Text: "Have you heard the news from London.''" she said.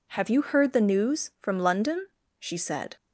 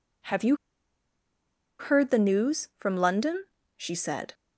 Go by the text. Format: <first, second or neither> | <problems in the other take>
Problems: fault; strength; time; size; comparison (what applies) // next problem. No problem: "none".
first | pauses between "you" and "heard"; strong; at 0.5 s; 1.2 s long